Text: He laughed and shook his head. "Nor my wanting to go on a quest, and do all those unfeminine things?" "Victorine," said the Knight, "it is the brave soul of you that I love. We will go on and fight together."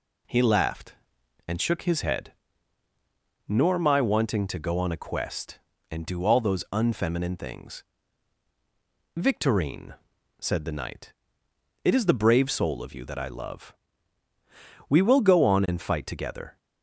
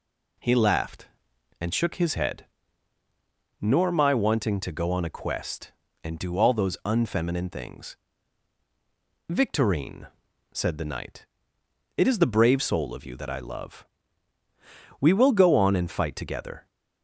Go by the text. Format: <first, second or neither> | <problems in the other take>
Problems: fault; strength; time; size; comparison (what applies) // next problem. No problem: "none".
neither | none